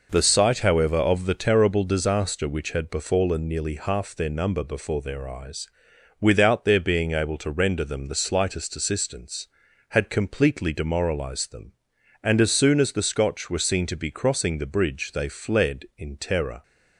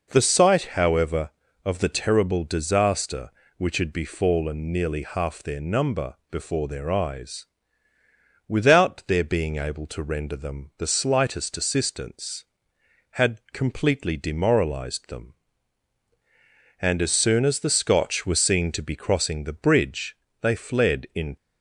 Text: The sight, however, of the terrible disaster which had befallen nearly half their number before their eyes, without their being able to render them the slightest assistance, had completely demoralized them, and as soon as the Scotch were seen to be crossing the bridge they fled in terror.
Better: first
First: none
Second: pauses between "bridge" and "they"; slight; at 20.1 s; 0.24 s long // stops before "terror"; at 21.3 s

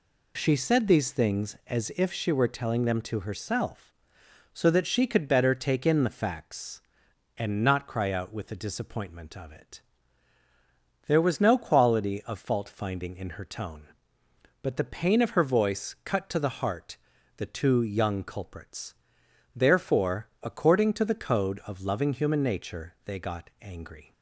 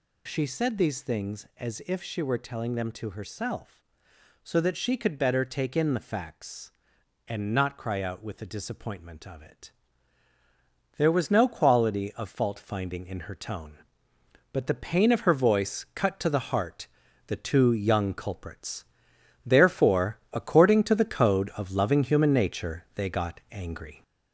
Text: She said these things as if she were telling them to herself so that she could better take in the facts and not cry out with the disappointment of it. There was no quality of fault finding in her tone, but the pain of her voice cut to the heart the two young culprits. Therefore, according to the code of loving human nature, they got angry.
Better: first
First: pauses between "heart" and "the"; at 16.9 s; 0.40 s long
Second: gets louder; noticeable; throughout; 5 dB // pauses between "heart" and "the"; at 16.8 s; 0.40 s long

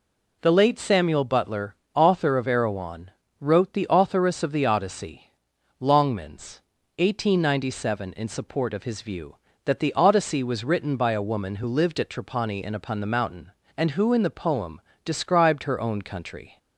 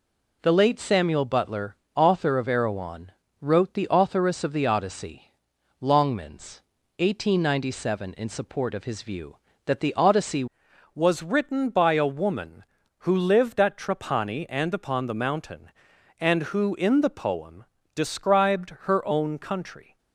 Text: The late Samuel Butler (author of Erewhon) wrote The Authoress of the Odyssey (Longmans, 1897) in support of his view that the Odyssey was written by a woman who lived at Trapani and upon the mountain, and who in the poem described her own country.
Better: first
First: pauses between "poem" and "described"; slight; at 14.7 s; 0.24 s long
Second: changes voice at "was"; from 10.9 s on; 9.0 s long // pauses between "poem" and "described"; slight; at 17.6 s; 0.28 s long

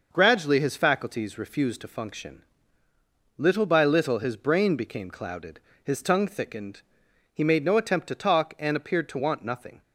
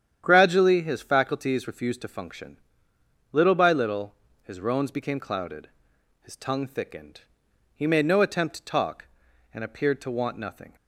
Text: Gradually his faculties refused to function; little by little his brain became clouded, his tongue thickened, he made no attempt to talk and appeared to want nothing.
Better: first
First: starts louder than the rest; noticeable; until 1.1 s; 6 dB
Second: starts louder than the rest; strong; until 1.2 s; 9.5 dB // pauses between "little" and "his"; slight; at 4.1 s; 0.26 s long // says "roans" for "brain"; at 4.5 s

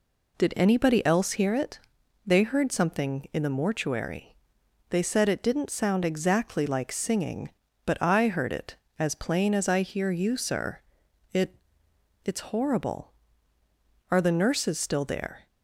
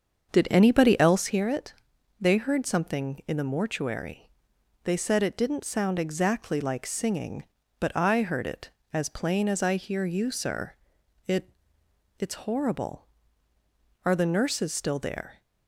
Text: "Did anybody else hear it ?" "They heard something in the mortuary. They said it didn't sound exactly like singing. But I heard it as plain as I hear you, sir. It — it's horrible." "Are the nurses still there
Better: first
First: none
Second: starts louder than the rest; until 1.3 s; 7 dB

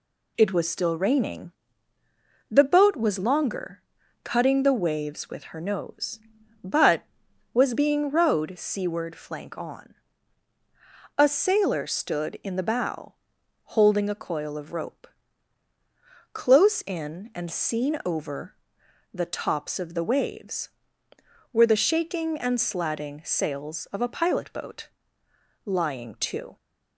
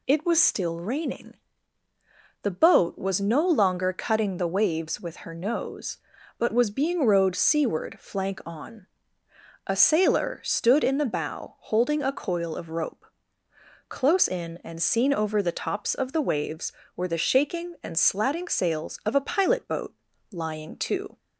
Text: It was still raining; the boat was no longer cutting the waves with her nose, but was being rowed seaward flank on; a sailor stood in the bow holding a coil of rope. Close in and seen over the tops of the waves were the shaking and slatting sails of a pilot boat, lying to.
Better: second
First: skips "no"; at 3.1 s // pauses between "longer" and "cutting"; at 3.8 s; 0.42 s long // pauses between "bow" and "holding"; noticeable; at 13.1 s; 0.62 s long // pauses between "over" and "the"; noticeable; at 18.5 s; 0.58 s long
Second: none

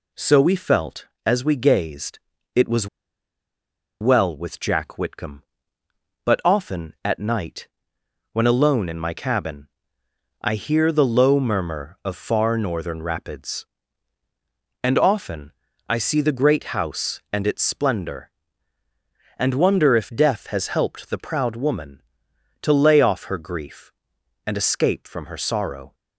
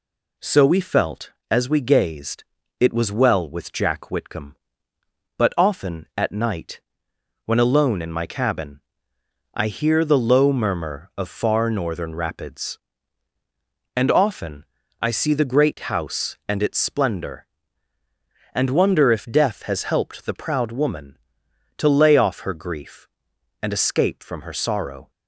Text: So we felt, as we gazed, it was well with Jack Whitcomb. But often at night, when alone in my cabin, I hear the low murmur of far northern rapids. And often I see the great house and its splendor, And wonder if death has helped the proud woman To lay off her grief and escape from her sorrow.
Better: second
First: pauses between "was" and "well"; at 2.8 s; 1.1 s long // pauses between "often" and "I"; slight; at 15.5 s; 0.36 s long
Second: pauses between "often" and "I"; slight; at 14.6 s; 0.36 s long

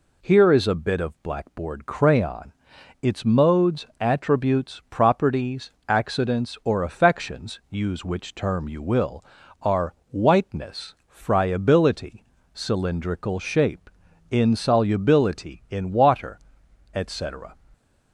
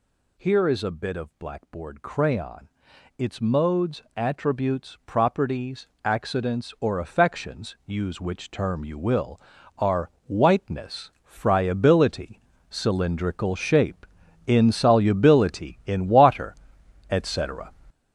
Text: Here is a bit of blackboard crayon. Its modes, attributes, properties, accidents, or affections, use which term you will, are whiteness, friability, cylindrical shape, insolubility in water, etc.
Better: first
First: pauses between "are" and "whiteness"; slight; at 9.9 s; 0.16 s long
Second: gets louder; strong; throughout; 8 dB // pauses between "are" and "whiteness"; slight; at 10.1 s; 0.16 s long

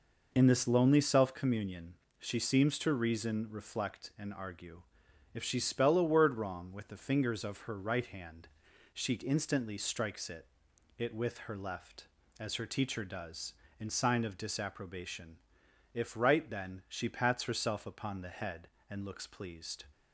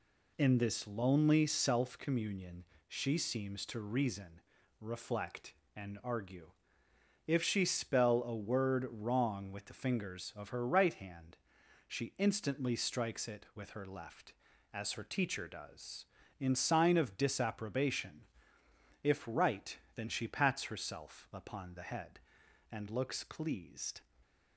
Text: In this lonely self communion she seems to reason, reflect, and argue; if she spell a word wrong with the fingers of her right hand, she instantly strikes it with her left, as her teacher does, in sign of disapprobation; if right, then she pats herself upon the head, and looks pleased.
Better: second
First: pauses between "communion" and "she"; slight; at 1.9 s; 0.24 s long // says "it" twice; at 10.9 s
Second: pauses between "communion" and "she"; slight; at 2.6 s; 0.24 s long

